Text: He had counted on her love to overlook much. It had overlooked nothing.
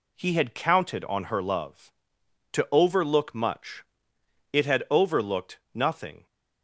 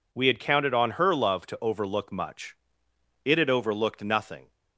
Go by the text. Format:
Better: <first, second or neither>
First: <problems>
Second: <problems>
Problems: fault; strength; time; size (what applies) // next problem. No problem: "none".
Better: first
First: none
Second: says "We" for "He"; at 0.1 s